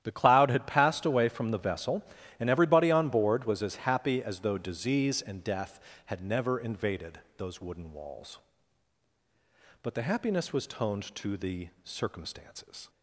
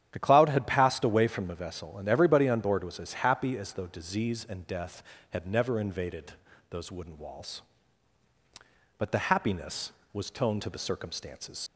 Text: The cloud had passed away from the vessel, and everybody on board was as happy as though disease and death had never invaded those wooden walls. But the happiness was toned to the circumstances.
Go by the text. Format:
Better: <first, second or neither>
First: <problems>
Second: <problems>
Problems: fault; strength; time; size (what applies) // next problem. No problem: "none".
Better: first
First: starts louder than the rest; strong; until 1.0 s; 11.5 dB // pauses between "invaded" and "those"; slight; at 7.1 s; 0.18 s long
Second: starts louder than the rest; strong; until 1.1 s; 10 dB // pauses between "invaded" and "those"; at 6.3 s; 0.38 s long // leaves "circumstances" unfinished; at 11.6 s; 65 ms